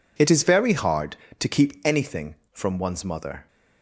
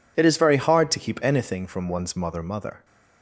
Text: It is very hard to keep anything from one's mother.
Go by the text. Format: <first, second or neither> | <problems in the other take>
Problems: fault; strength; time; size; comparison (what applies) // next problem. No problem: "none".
first | says "mother" twice; at 2.4 s